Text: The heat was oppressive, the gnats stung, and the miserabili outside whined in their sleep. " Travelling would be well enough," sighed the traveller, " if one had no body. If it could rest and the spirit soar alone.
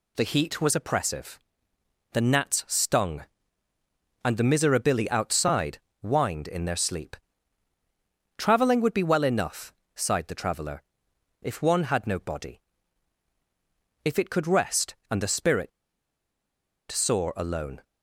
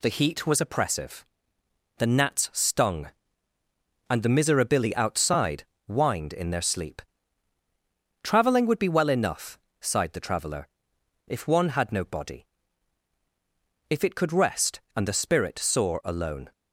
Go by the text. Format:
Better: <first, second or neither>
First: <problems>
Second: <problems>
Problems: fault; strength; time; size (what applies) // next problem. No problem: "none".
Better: second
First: pauses between "outside" and "whined"; slight; at 5.7 s; 0.22 s long // pauses between "spirit" and "soar"; at 15.7 s; 1.2 s long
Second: pauses between "outside" and "whined"; slight; at 5.6 s; 0.22 s long